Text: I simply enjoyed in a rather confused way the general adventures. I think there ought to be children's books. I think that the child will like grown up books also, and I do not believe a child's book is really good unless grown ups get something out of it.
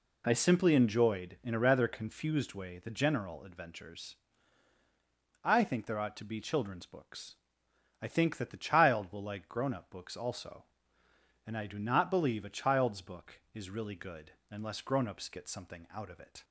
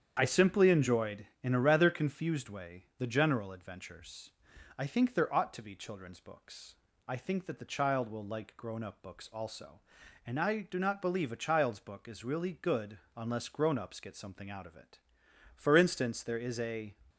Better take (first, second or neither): first